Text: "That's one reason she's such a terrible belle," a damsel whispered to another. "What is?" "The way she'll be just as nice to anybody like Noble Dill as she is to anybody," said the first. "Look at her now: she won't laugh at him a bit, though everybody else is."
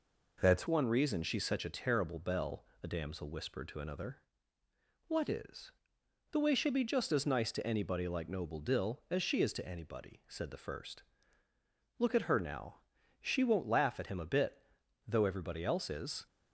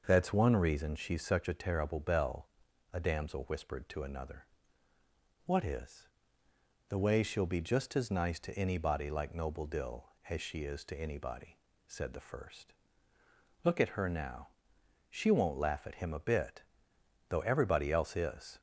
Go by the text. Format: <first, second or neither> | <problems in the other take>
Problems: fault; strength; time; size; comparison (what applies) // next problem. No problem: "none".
second | changes voice at "one"; from 0.6 s on; 15.6 s long